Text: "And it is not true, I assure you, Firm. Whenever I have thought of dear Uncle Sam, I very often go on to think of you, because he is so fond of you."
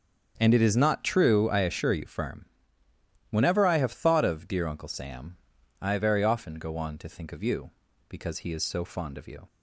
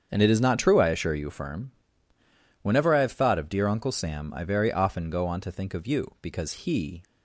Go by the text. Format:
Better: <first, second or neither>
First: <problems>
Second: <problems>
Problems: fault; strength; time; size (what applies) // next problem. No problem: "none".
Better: first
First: starts louder than the rest; strong; until 1.3 s; 7.5 dB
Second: starts louder than the rest; strong; until 1.1 s; 7.5 dB // stops before "is so fond of you"; at 7.0 s